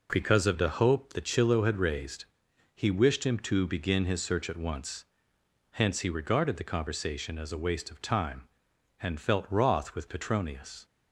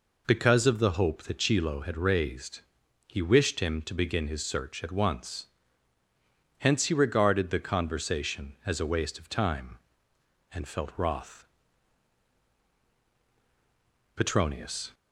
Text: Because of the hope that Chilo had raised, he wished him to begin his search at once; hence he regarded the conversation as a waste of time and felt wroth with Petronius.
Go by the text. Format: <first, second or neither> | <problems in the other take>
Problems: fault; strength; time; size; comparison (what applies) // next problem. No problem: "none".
first | skips "with"; at 12.8 s